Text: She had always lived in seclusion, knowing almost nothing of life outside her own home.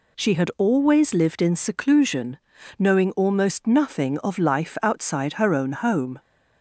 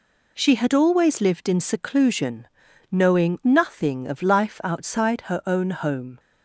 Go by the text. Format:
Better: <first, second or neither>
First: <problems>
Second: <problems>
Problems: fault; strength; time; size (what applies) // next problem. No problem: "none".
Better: first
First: none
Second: skips "almost"; at 3.4 s